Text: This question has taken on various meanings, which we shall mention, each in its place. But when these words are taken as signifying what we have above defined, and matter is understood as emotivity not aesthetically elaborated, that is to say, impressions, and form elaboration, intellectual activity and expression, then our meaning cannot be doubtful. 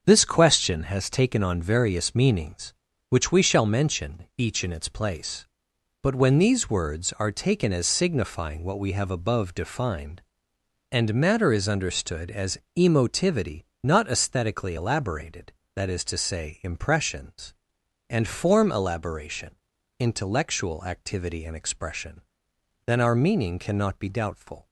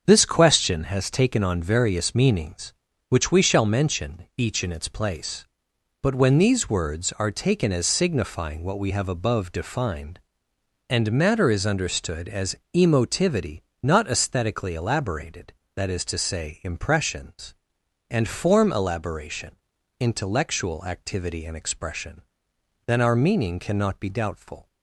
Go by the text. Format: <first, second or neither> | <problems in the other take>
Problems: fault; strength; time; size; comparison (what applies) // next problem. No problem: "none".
neither | starts louder than the rest; the same in both // pauses between "as" and "emotivity"; slight; the same in both // pauses between "emotivity" and "not"; slight; the same in both